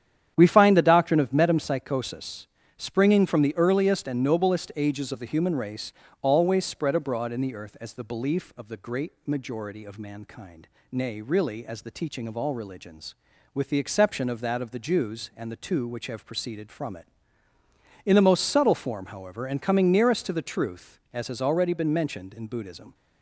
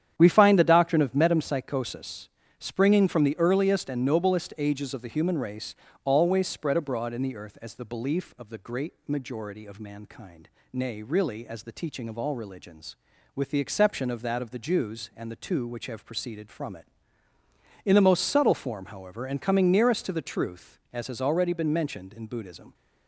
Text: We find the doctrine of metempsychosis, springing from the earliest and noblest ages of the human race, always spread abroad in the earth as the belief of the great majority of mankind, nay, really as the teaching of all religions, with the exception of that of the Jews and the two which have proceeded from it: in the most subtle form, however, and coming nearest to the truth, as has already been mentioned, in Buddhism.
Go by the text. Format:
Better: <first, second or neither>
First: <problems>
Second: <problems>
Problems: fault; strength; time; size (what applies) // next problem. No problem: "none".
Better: neither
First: starts louder than the rest; strong; until 1.3 s; 9.5 dB // pauses between "great" and "majority"; slight; at 9.1 s; 0.16 s long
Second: starts louder than the rest; strong; until 1.1 s; 9.5 dB // pauses between "great" and "majority"; slight; at 8.9 s; 0.16 s long